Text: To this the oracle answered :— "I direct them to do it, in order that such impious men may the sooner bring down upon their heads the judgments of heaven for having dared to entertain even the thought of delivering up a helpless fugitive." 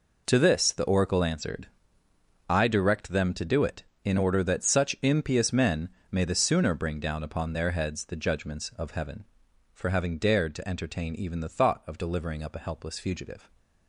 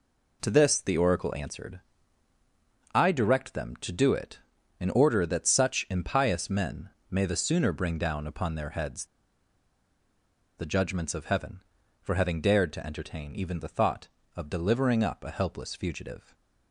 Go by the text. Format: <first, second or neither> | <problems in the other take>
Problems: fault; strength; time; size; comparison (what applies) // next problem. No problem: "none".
first | pauses between "men" and "may"; slight; at 6.8 s; 0.22 s long; slight in the first // pauses between "heads" and "the"; strong; at 9.0 s; 1.5 s long // stays silent after the last word; slight; from 16.2 s on; 0.5 s long